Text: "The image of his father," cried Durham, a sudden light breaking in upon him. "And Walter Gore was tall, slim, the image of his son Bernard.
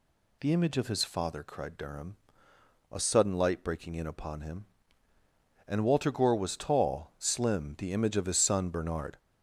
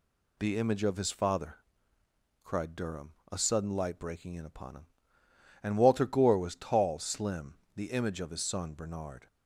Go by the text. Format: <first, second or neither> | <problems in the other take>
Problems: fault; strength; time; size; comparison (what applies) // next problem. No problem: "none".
neither | none